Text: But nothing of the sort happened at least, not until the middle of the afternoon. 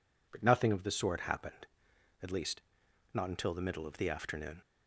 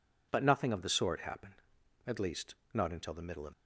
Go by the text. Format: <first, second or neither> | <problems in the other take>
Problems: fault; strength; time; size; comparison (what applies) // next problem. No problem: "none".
first | stops before "the afternoon"; at 3.5 s